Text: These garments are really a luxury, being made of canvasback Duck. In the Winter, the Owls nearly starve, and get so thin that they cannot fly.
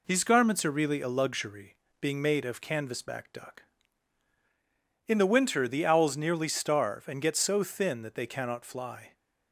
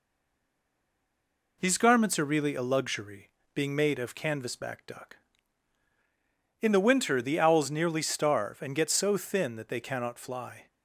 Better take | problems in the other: first | stays silent before the first word; noticeable; until 1.6 s; 1.6 s long

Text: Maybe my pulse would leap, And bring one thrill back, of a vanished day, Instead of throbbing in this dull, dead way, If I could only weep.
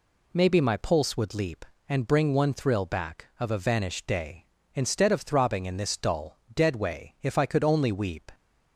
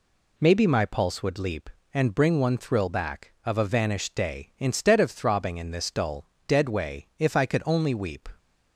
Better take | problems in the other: neither | none

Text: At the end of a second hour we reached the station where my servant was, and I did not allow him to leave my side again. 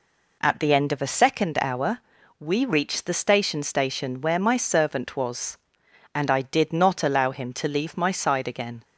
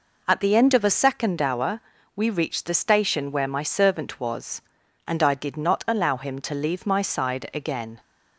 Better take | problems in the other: second | pauses between "hour" and "we"; at 2.0 s; 0.38 s long; slight in the second // says "station" twice; at 3.6 s

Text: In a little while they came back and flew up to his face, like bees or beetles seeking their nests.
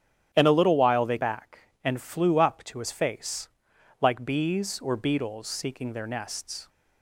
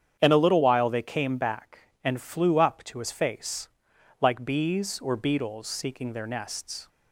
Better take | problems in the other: second | starts louder than the rest; strong; until 1.3 s; 11 dB; strong in the second // skips "came"; at 1.1 s

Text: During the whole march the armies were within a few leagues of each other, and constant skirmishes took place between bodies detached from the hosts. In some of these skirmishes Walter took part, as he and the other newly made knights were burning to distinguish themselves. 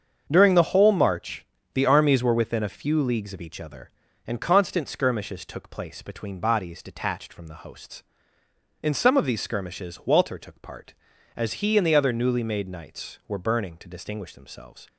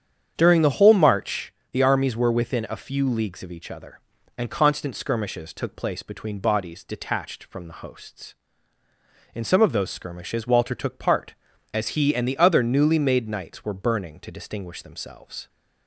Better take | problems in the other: first | starts louder than the rest; strong; until 1.3 s; 8.5 dB; also in the first // pauses between "march" and "the"; slight; at 1.5 s; 0.20 s long; slight in the first // says "those" for "these"; at 9.7 s

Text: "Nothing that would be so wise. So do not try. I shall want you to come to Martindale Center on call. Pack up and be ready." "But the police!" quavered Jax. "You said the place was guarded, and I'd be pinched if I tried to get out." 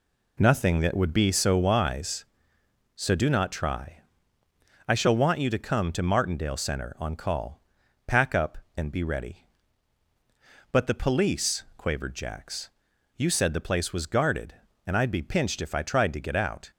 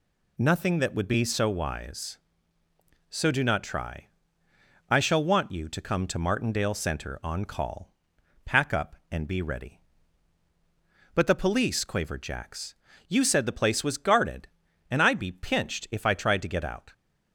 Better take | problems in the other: neither | none

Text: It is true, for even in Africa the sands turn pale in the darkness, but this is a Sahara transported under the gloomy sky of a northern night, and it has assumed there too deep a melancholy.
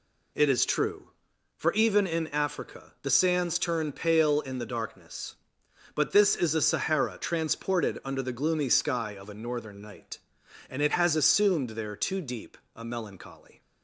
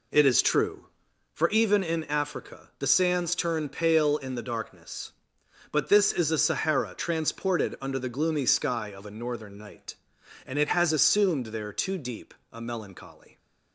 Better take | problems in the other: first | starts louder than the rest; slight; until 1.5 s; 3 dB // pauses between "deep" and "a"; slight; at 12.3 s; 0.18 s long; slight in the first

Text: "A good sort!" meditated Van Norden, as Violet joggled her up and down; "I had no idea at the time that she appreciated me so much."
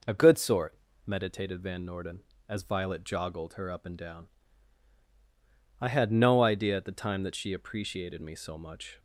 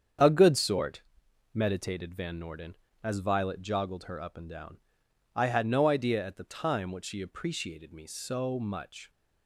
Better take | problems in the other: first | starts louder than the rest; strong; until 1.7 s; 7.5 dB // says "what" for "that"; at 6.9 s

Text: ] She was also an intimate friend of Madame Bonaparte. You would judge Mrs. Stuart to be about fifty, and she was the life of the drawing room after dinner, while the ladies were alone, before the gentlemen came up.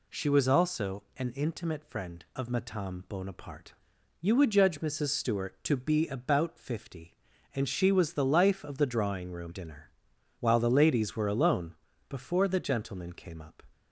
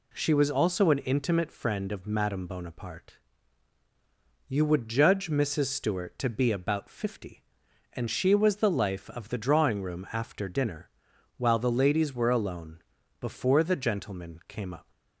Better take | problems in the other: second | skips "after"; at 9.5 s

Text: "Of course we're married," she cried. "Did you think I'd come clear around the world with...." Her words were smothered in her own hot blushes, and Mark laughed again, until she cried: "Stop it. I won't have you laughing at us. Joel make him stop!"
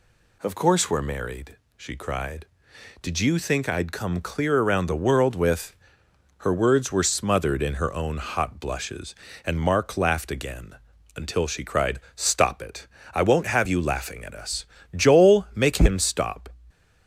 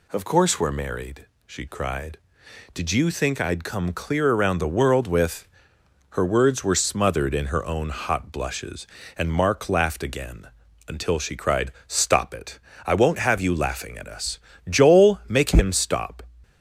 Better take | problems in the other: neither | none

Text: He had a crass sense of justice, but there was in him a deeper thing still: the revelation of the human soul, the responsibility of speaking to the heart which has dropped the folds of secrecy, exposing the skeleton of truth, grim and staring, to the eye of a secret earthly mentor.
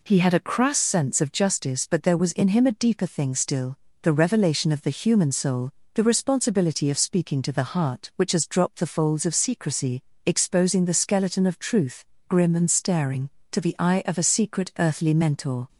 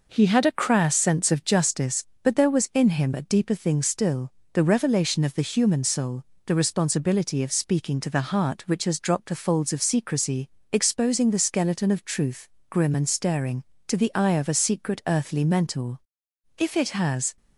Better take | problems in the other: first | goes on to say "If it has"; noticeable; from 16.5 s on; 0.78 s long

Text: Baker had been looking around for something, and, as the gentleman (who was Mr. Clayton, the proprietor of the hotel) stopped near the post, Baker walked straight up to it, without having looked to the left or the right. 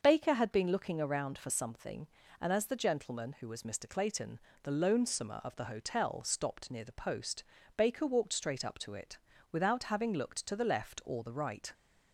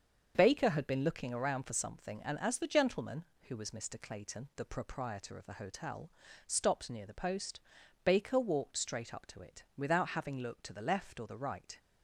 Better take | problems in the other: second | starts louder than the rest; until 1.0 s; 6 dB; also in the second // says "lonesomer" for "proprietor"; at 4.7 s

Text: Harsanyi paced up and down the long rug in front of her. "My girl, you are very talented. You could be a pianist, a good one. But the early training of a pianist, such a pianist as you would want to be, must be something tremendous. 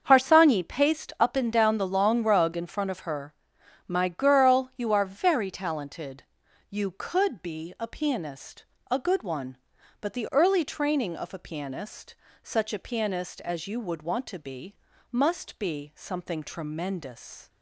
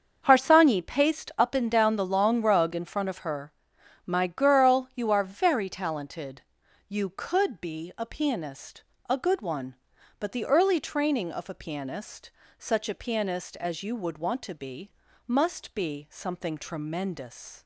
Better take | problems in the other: neither | starts louder than the rest; the same in both

